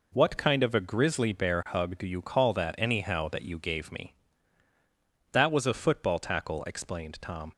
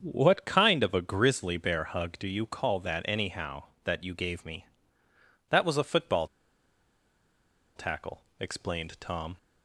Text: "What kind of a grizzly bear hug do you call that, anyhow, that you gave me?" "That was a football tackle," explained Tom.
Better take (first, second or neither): first